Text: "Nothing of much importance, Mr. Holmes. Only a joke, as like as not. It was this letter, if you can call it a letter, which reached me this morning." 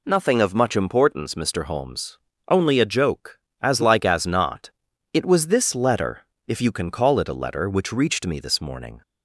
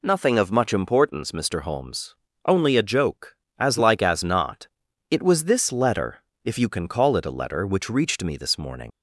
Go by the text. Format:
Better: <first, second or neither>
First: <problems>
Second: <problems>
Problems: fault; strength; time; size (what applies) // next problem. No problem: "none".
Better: first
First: none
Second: leaves "morning" unfinished; at 8.9 s; 85 ms